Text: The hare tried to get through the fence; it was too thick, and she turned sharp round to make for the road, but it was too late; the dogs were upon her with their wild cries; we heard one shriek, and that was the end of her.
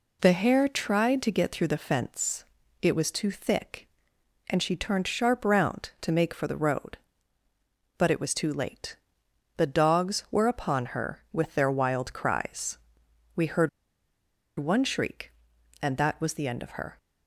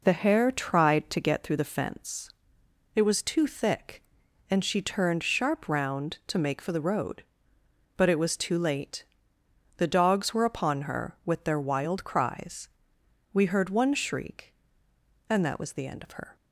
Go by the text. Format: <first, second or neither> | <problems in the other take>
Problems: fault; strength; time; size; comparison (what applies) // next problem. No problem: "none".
second | pauses between "heard" and "one"; noticeable; at 13.6 s; 0.90 s long